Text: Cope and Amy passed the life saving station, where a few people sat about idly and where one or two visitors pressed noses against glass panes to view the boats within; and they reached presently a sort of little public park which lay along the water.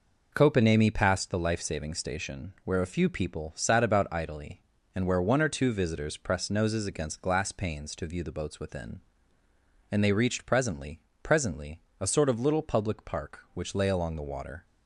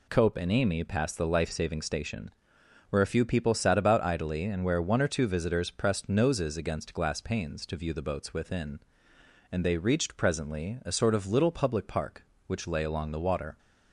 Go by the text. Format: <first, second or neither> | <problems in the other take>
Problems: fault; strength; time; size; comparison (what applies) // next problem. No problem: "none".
second | says "presently" twice; at 11.2 s